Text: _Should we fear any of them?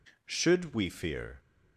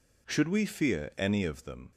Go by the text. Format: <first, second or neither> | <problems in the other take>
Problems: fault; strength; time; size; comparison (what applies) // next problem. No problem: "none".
second | stops before "any of them"; at 1.3 s